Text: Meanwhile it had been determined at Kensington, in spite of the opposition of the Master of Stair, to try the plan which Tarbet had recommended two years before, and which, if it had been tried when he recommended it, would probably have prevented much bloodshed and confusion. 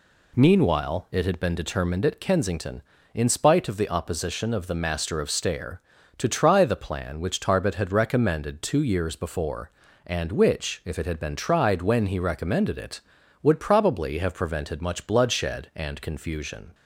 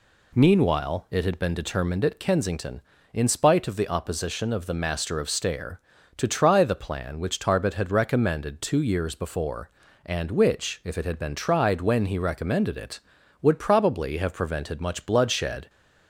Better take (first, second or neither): first